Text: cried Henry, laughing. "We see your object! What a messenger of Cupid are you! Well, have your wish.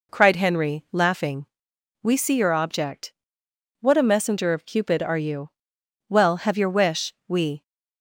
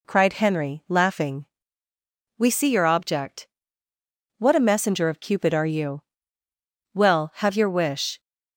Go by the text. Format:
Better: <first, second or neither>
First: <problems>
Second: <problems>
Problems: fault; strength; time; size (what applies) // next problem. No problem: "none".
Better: second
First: goes on to say "We"; slight; from 7.2 s on; 0.34 s long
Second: none